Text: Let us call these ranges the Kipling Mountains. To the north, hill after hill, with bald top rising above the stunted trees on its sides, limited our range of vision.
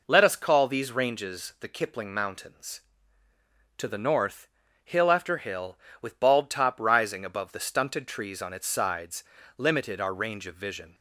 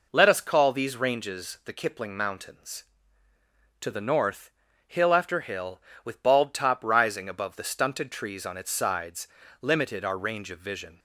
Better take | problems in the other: neither | none

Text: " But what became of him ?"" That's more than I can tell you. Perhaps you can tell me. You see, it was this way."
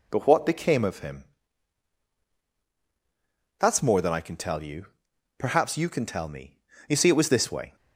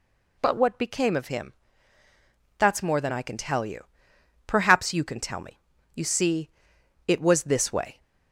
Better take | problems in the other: second | changes voice at "But"; from 0.1 s on; 7.6 s long

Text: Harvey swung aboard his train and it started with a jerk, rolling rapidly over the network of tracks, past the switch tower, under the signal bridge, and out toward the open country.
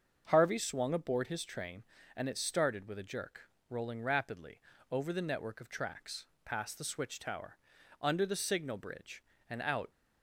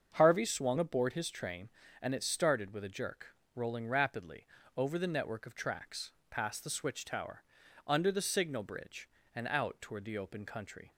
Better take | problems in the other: second | starts louder than the rest; until 1.2 s; 6.5 dB; also in the second // pauses between "rapidly" and "over"; slight; at 4.5 s; 0.32 s long; slight in the second // stops before "toward the open country"; at 9.9 s

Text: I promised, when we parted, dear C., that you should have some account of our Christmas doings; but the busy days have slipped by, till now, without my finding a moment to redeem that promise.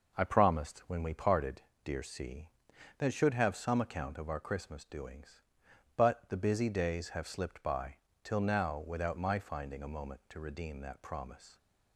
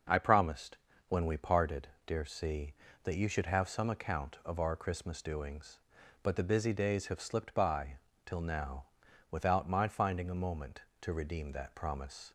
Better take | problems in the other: second | skips "you"; at 3.1 s

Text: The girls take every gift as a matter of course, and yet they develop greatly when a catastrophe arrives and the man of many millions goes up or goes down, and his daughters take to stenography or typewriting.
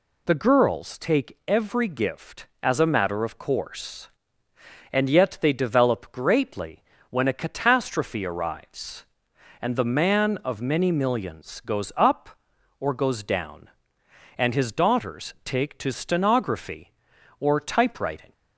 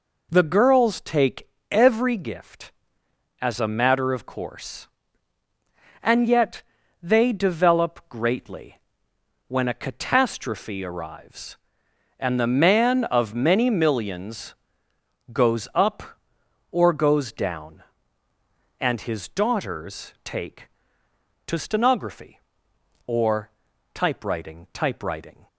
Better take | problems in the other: first | pauses between "take" and "every"; slight; at 1.4 s; 0.24 s long // pauses between "yet" and "they"; at 6.6 s; 0.40 s long // pauses between "greatly" and "when"; noticeable; at 8.7 s; 0.70 s long; slight in the first // pauses between "millions" and "goes"; noticeable; at 14.5 s; 0.80 s long // pauses between "or" and "typewriting"; noticeable; at 23.4 s; 0.46 s long // says "typewriting" twice; at 24.7 s

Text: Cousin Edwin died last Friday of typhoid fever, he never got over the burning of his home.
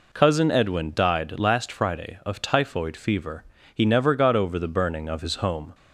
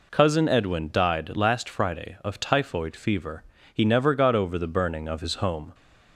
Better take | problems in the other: neither | none

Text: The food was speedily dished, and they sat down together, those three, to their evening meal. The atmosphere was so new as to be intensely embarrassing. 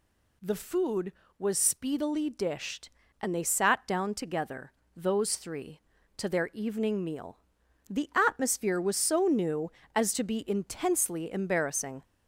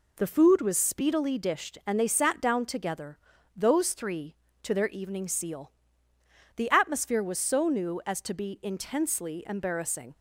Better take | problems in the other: first | says "seal" for "meal"; at 5.2 s

